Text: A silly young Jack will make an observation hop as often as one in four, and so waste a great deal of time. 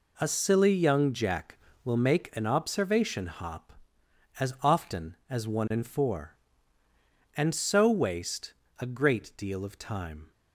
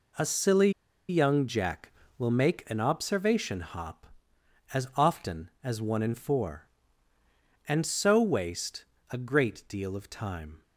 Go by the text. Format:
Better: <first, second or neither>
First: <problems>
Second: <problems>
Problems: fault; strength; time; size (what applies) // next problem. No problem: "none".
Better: first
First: pauses between "waste" and "a"; slight; at 8.5 s; 0.24 s long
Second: pauses between "silly" and "young"; at 0.6 s; 0.38 s long // pauses between "waste" and "a"; slight; at 8.8 s; 0.24 s long